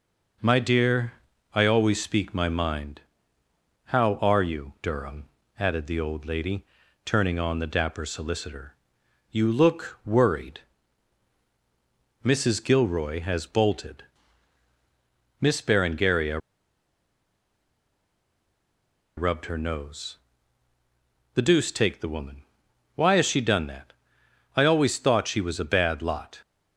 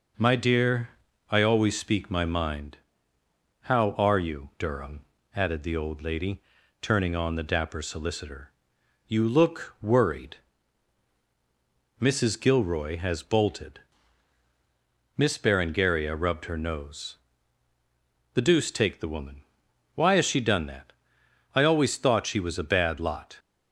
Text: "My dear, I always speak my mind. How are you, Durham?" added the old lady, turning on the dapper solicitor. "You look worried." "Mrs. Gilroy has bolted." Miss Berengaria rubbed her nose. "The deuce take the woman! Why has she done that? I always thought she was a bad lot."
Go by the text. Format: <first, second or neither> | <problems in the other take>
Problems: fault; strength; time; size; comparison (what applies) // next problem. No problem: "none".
second | pauses between "Berengaria" and "rubbed"; strong; at 16.3 s; 2.7 s long